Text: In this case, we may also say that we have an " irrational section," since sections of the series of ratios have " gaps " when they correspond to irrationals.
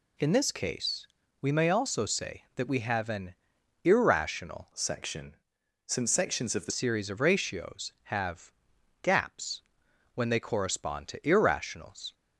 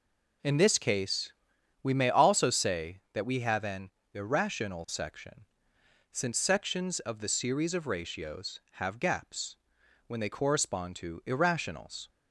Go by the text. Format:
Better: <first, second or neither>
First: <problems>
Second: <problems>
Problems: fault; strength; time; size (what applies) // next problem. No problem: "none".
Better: second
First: changes voice from "section" to "the"; from 4.7 to 6.7 s; 2.0 s long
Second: none